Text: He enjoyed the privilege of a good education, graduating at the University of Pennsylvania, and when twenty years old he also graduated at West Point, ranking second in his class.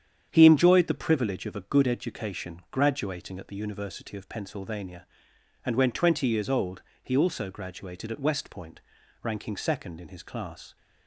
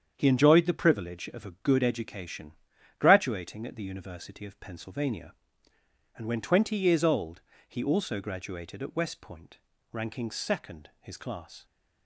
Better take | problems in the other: first | starts louder than the rest; strong; until 1.1 s; 8 dB; strong in the first // pauses between "old" and "he"; slight; at 7.4 s; 0.26 s long; slight in the first // skips "in"; at 10.9 s

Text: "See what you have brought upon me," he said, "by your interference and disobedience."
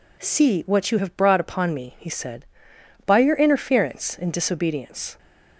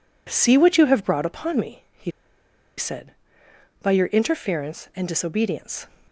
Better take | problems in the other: first | pauses between "he" and "said"; noticeable; at 2.1 s; 0.67 s long

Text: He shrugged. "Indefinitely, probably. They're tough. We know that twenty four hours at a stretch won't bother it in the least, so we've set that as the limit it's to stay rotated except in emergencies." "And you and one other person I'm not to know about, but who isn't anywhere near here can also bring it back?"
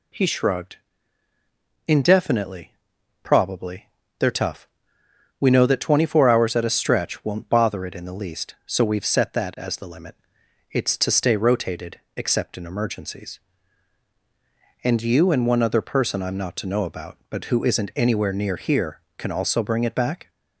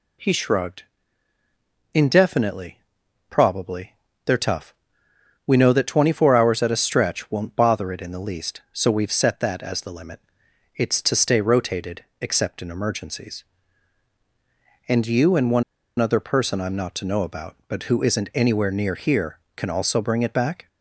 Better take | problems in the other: first | pauses between "limit" and "it's"; noticeable; at 10.1 s; 0.56 s long; noticeable in the first // pauses between "rotated" and "except"; slight; at 12.0 s; 0.16 s long; slight in the first // pauses between "one" and "other"; at 15.6 s; 0.36 s long

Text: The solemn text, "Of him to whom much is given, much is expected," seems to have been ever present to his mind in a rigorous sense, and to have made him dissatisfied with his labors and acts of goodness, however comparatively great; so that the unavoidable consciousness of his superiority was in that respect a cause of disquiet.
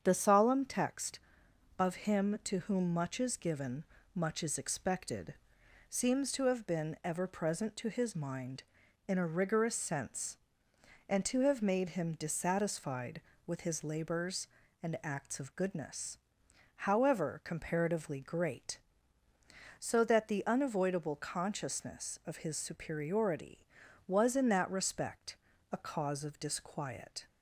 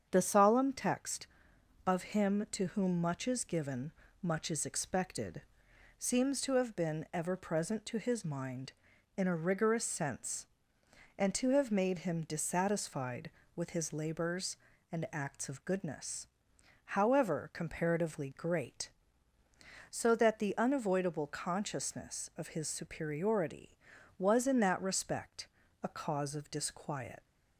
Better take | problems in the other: first | starts louder than the rest; strong; until 1.1 s; 7.5 dB; strong in the first // pauses between "respect" and "a"; at 25.4 s; 0.38 s long; also in the first // leaves "disquiet" unfinished; at 27.2 s; 110 ms

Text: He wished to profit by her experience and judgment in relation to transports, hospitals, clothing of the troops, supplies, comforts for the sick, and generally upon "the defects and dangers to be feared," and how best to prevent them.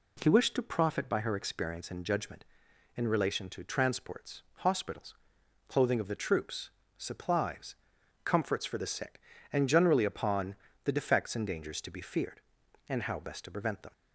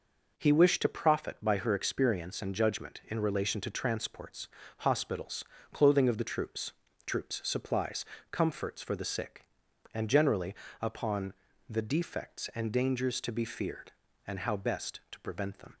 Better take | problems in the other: first | says "troops" twice; at 7.0 s // pauses between "generally" and "upon"; slight; at 10.5 s; 0.26 s long // pauses between "upon" and "the"; slight; at 11.3 s; 0.34 s long; slight in the first

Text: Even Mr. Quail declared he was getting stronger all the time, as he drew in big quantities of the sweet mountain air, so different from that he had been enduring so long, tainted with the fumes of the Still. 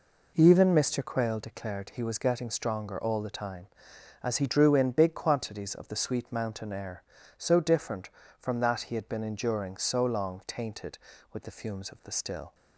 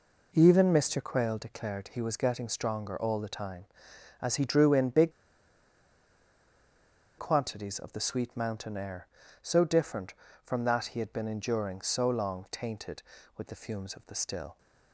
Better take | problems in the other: first | pauses between "big" and "quantities"; strong; at 5.1 s; 2.0 s long

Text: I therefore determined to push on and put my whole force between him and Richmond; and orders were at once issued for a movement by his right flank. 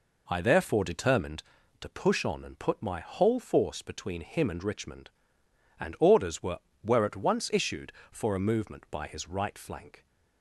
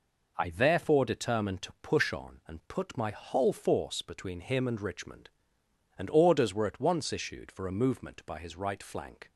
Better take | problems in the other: second | says "were" twice; at 6.8 s

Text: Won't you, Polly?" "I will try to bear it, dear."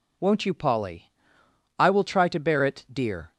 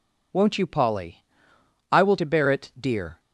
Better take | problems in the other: first | skips "try"; at 2.1 s

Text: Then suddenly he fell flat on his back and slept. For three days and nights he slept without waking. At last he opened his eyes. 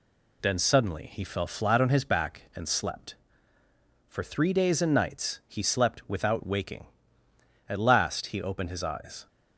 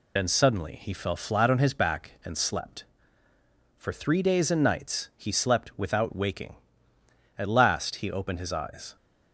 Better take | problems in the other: first | loses the start of "Then"; at 0.1 s; 65 ms

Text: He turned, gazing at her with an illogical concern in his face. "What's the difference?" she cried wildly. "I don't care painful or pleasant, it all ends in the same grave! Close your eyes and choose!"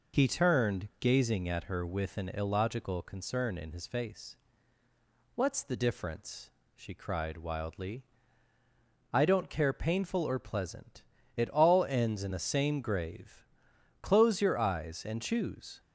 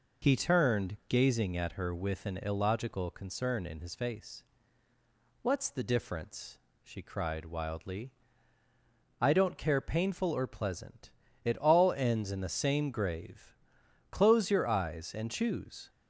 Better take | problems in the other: neither | none

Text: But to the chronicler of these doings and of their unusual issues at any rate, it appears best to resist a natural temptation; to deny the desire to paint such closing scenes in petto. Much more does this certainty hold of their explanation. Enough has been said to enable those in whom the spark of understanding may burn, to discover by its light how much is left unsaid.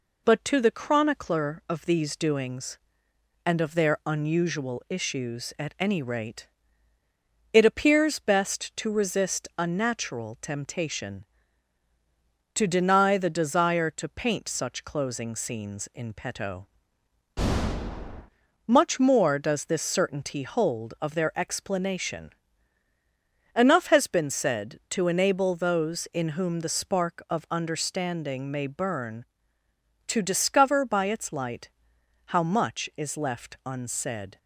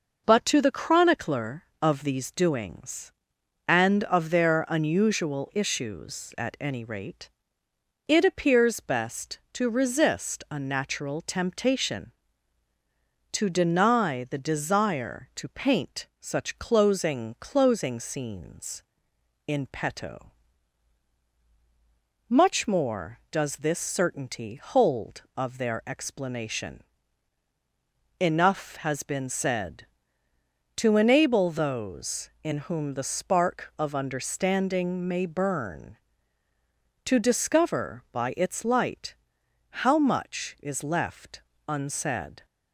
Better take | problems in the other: first | says "closing" twice; at 17.3 s // pauses between "light" and "how"; noticeable; at 39.1 s; 0.70 s long; noticeable in the first // pauses between "left" and "unsaid"; slight; at 41.4 s; 0.28 s long

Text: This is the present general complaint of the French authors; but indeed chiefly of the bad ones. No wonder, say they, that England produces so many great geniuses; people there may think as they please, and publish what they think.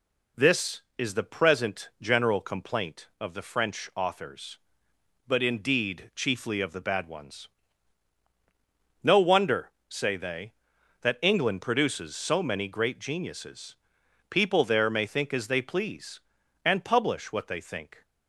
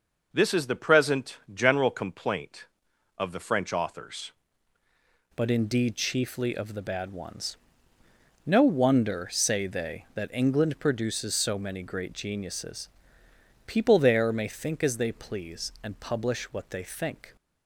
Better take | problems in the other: first | pauses between "present" and "general"; slight; at 1.3 s; 0.16 s long // changes voice at "but"; from 5.3 s on; 12.0 s long

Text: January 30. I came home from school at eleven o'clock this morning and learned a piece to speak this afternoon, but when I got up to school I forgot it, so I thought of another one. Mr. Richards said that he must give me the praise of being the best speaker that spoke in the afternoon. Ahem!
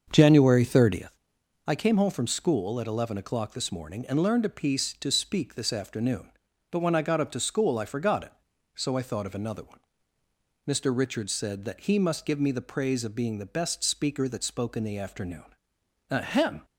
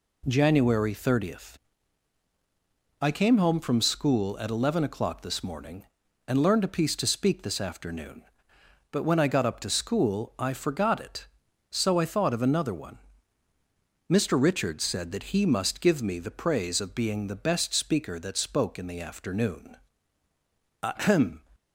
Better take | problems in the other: second | starts louder than the rest; until 1.1 s; 7 dB

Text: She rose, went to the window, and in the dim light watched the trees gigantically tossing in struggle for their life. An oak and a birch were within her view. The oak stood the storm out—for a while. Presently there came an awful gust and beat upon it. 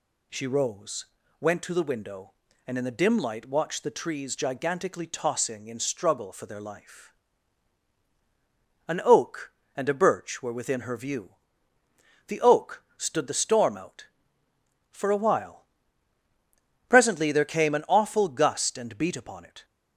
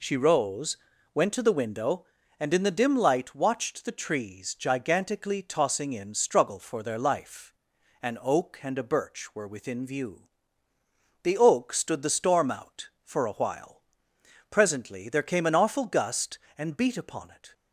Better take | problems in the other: first | skips "her"; at 9.8 s

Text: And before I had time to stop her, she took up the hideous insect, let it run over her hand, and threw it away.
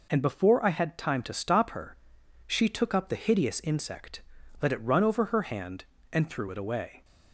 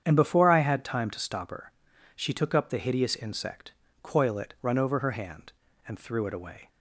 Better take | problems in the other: first | starts louder than the rest; strong; until 1.0 s; 8.5 dB // says "coil" for "let"; at 4.0 s

